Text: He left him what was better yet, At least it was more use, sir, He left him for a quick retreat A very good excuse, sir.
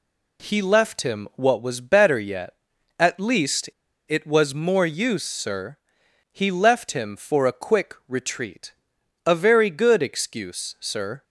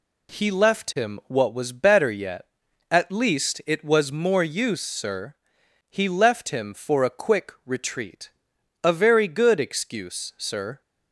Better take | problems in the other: second | pauses between "least" and "it"; at 3.6 s; 0.40 s long // pauses between "retreat" and "A"; noticeable; at 8.7 s; 0.52 s long; noticeable in the second

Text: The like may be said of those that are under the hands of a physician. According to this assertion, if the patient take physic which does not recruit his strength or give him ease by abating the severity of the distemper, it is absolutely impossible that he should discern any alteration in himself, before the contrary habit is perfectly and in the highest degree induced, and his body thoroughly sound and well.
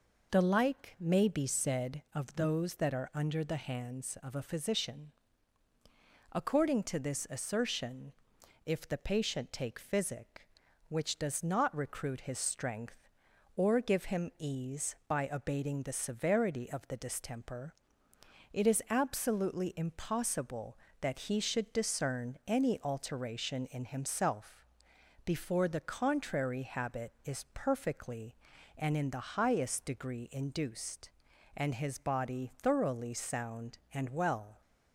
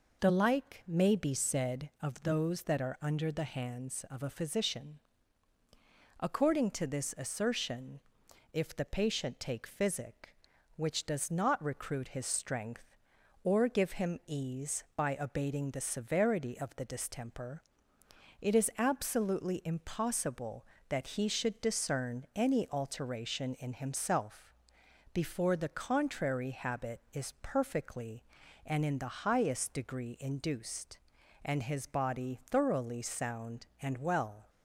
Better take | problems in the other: neither | none

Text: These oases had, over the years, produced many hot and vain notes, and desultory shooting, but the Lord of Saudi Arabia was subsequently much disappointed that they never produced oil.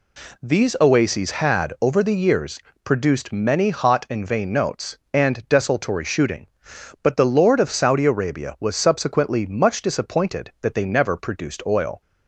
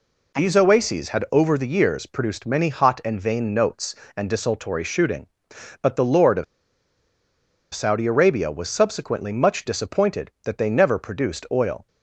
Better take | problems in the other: first | pauses between "of" and "Saudi"; strong; at 6.4 s; 1.3 s long

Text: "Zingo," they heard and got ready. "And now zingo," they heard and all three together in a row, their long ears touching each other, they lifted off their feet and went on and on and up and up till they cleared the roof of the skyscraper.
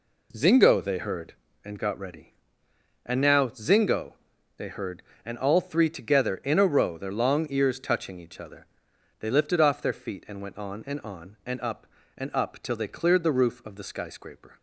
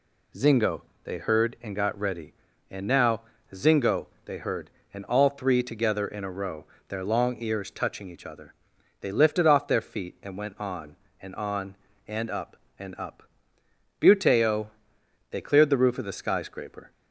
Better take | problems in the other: first | pauses between "now" and "zingo"; slight; at 3.2 s; 0.28 s long // says "buteo" for "till"; at 14.0 s

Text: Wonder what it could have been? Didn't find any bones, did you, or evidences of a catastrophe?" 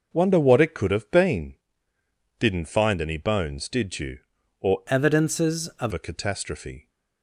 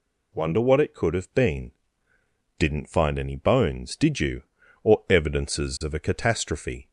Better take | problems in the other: second | changes voice from "evidences" to "of"; from 4.8 to 5.9 s; 1.1 s long

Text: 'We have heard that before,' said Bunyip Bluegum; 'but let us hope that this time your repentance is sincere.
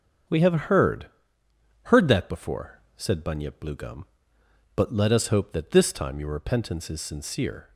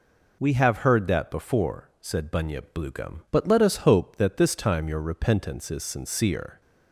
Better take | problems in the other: second | starts louder than the rest; until 2.0 s; 7 dB // says "heard" twice; at 1.8 s

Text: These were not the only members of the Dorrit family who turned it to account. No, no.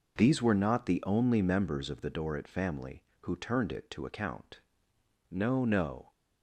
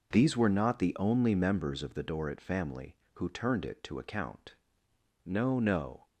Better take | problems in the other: neither | none

